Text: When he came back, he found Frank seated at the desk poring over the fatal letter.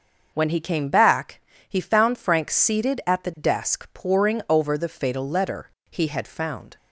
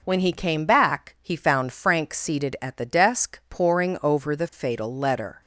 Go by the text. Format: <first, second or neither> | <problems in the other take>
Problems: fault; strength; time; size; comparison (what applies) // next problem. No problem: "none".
second | starts louder than the rest; noticeable; until 1.3 s; 6 dB // goes on to say "He had found"; noticeable; from 5.9 s on; 0.86 s long